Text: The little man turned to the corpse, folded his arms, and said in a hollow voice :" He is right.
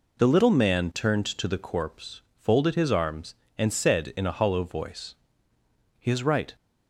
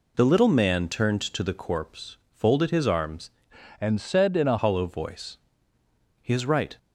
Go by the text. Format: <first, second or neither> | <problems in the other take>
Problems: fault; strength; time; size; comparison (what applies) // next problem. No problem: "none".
first | changes voice from "and" to "a"; from 3.7 to 4.5 s; 0.8 s long